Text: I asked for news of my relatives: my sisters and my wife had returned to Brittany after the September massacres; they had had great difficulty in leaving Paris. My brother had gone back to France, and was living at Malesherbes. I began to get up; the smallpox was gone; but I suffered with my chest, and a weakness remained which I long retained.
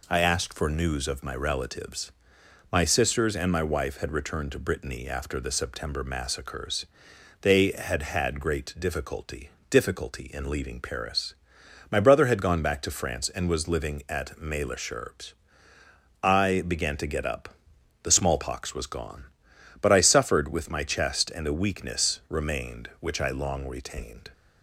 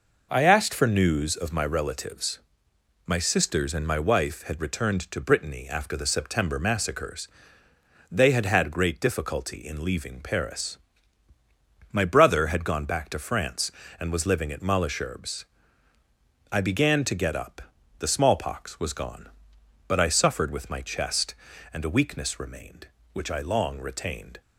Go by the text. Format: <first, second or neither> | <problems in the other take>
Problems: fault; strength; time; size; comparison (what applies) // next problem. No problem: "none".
second | says "difficulty" twice; at 9.7 s